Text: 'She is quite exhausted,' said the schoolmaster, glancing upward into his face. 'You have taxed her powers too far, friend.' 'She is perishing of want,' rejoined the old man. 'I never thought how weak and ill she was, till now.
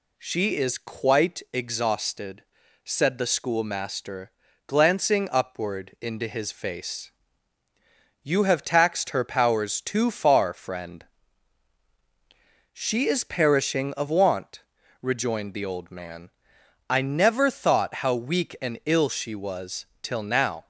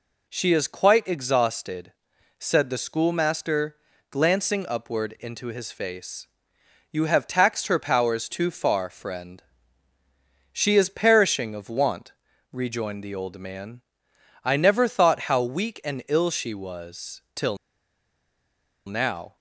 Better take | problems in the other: first | pauses between "till" and "now"; strong; at 17.5 s; 1.3 s long

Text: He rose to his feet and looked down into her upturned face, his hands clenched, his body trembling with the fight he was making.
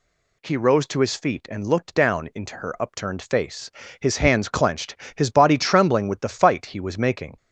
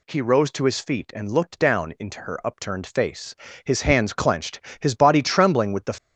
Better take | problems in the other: first | stops before "fight he was making"; at 5.9 s

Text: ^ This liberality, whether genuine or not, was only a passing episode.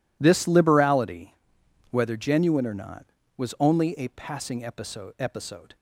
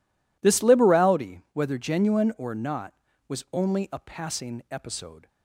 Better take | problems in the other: second | says "episode" twice; at 5.1 s

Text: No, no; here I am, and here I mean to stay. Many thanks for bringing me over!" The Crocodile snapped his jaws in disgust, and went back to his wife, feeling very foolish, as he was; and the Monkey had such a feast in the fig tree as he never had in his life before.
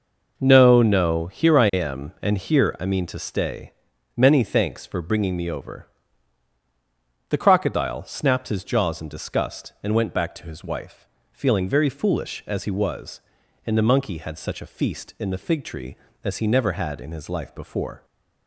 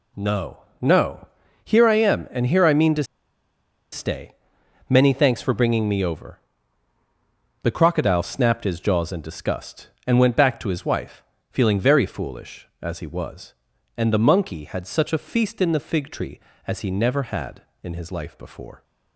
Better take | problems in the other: first | pauses between "to" and "stay"; noticeable; at 3.0 s; 0.89 s long

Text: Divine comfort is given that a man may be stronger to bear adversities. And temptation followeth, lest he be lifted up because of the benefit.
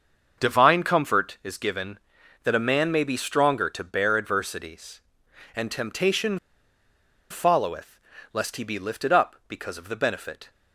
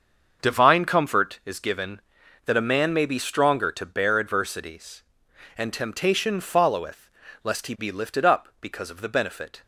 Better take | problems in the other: second | starts louder than the rest; until 1.4 s; 6.5 dB; also in the second // pauses between "temptation" and "followeth"; noticeable; at 6.3 s; 0.92 s long

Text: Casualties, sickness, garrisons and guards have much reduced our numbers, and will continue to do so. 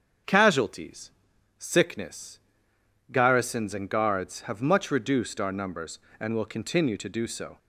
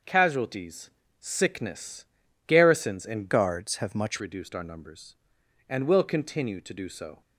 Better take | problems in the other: first | starts louder than the rest; until 1.3 s; 6 dB; also in the first // changes voice from "guards" to "much"; from 3.3 to 4.1 s; 0.8 s long

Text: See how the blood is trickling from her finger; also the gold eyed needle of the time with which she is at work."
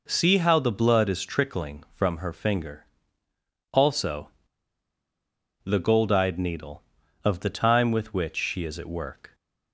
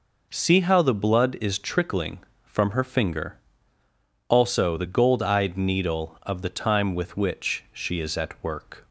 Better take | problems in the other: second | pauses between "also" and "the"; strong; at 4.3 s; 1.3 s long

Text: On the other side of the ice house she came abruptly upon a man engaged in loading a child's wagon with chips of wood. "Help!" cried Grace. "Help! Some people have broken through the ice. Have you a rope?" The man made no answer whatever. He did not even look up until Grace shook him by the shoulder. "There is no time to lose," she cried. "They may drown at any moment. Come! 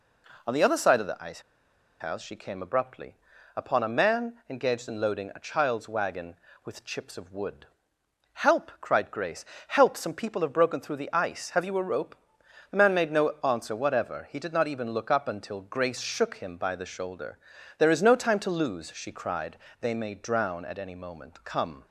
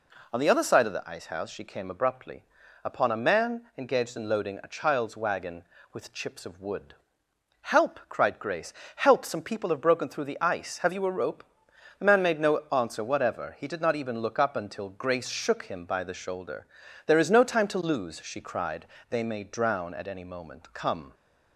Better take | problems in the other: second | pauses between "ice" and "house"; noticeable; at 1.4 s; 0.59 s long // pauses between "abruptly" and "upon"; at 3.1 s; 0.40 s long; also in the second

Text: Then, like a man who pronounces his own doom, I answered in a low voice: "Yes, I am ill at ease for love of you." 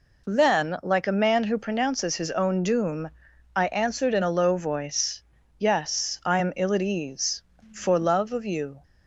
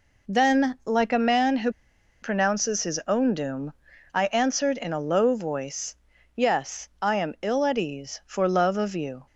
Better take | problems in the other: first | pauses between "who" and "pronounces"; noticeable; at 1.7 s; 0.51 s long

